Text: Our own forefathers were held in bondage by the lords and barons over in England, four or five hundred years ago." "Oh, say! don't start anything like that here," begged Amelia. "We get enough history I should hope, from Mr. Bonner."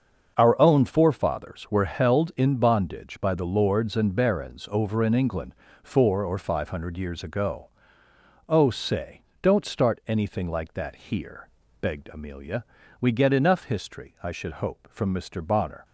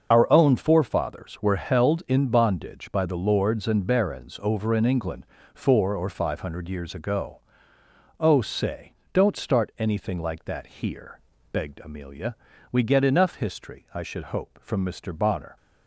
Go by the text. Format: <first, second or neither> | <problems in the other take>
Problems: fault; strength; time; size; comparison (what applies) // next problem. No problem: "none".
first | loses the start of "Our"; at 0.1 s; 30 ms // starts louder than the rest; until 1.1 s; 6.5 dB; also in the first